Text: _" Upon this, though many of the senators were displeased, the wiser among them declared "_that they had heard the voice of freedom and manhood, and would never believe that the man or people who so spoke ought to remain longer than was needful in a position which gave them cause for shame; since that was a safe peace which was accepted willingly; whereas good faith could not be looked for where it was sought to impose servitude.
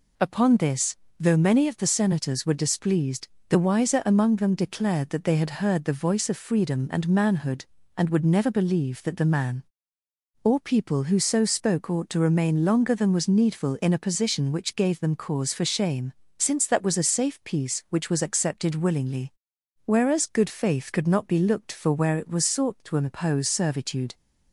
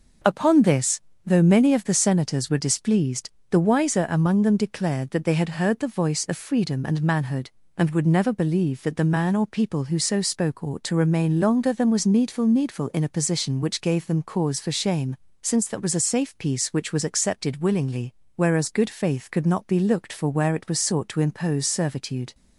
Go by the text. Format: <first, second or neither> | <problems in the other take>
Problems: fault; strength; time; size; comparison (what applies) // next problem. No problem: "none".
first | says "needful" twice; at 12.4 s